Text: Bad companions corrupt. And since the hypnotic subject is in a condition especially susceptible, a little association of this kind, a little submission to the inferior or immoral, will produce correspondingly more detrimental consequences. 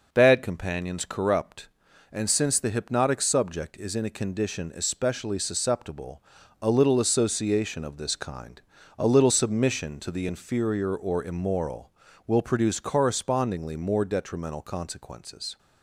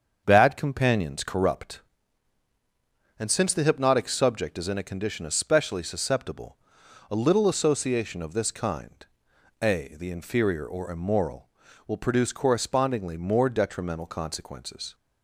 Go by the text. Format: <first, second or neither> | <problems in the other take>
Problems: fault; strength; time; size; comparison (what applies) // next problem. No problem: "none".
first | starts louder than the rest; until 1.2 s; 7 dB // skips "little submission to"; at 9.9 s